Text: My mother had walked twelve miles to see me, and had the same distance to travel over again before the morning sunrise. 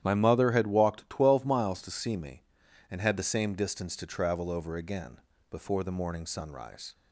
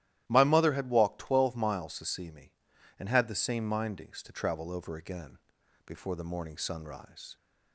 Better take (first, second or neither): first